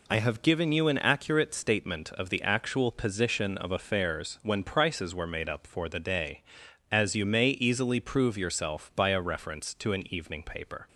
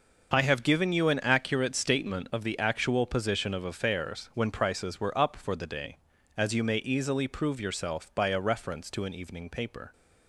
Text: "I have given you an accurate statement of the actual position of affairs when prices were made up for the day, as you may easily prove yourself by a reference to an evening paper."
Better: first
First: none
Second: skips "made"; at 5.1 s

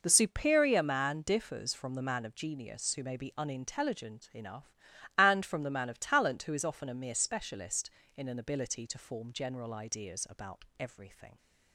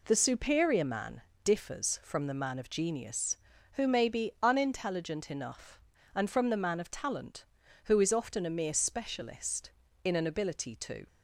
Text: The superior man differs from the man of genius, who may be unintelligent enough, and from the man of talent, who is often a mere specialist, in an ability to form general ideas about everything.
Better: first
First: none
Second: pauses between "man" and "differs"; slight; at 1.2 s; 0.24 s long // stops before "form general ideas about everything"; at 11.0 s

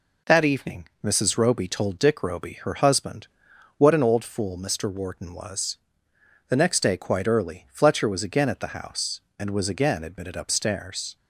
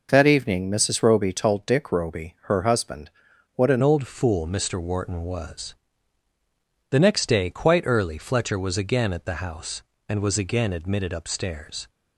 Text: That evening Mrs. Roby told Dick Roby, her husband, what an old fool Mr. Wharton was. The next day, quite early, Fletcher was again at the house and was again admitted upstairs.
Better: first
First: none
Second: changes voice at "old"; from 3.8 s on; 8.0 s long

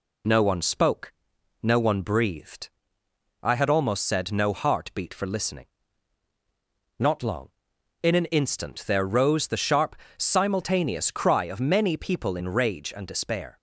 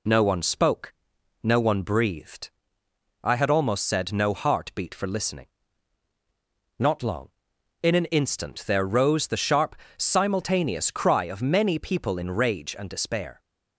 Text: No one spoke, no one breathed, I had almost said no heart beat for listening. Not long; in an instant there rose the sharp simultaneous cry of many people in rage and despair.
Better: neither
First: pauses between "sharp" and "simultaneous"; slight; at 9.9 s; 0.24 s long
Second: pauses between "sharp" and "simultaneous"; slight; at 9.7 s; 0.24 s long

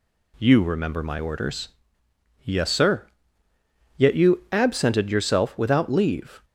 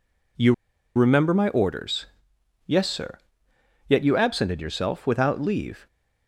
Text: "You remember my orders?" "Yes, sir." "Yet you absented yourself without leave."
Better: first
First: none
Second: pauses between "You" and "remember"; at 0.5 s; 0.42 s long

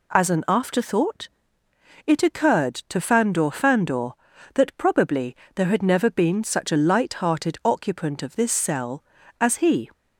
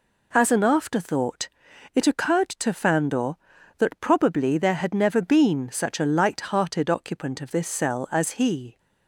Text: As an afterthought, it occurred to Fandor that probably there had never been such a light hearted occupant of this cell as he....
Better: second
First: says "Fandor" twice; at 3.4 s // pauses between "probably" and "there"; slight; at 5.3 s; 0.20 s long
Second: none

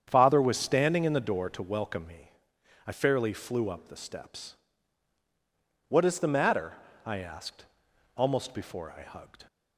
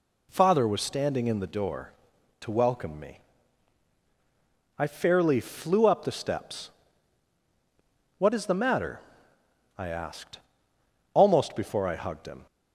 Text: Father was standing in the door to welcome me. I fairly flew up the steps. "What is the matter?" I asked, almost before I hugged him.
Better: second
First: starts louder than the rest; strong; until 1.0 s; 8 dB // stops before "him"; at 9.4 s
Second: none

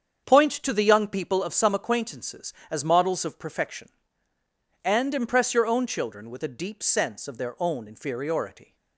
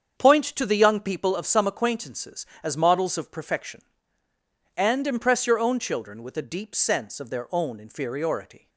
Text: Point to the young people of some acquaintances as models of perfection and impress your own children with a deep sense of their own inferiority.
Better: neither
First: starts louder than the rest; strong; until 1.2 s; 7.5 dB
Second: starts louder than the rest; strong; until 1.1 s; 7.5 dB

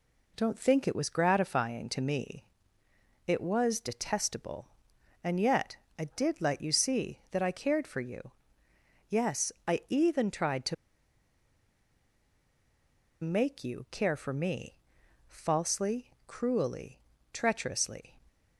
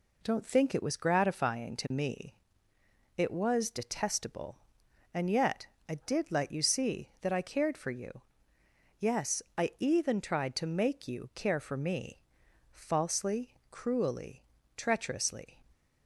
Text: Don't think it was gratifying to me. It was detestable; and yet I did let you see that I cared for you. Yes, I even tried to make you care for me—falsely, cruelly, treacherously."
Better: second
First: pauses between "yet" and "I"; slight; at 5.7 s; 0.22 s long // pauses between "to" and "make"; strong; at 10.7 s; 2.4 s long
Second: pauses between "yet" and "I"; slight; at 5.6 s; 0.22 s long

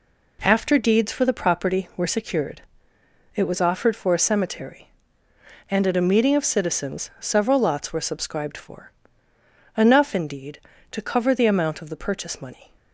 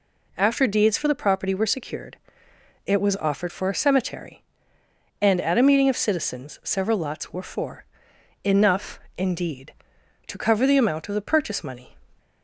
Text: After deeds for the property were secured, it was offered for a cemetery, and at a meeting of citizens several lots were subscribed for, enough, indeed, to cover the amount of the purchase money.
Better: first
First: none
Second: skips "subscribed"; at 7.4 s

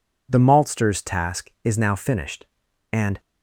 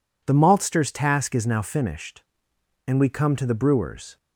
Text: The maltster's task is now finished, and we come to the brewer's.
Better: second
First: stops before "we come to the brewer's"; at 3.1 s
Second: none

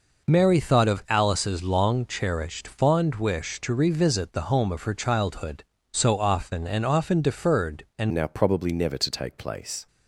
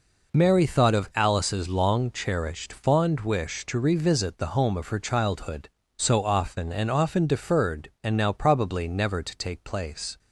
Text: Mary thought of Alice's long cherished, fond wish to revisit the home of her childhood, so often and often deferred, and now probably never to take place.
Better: second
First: changes voice at "now"; from 8.1 s on; 1.7 s long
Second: none

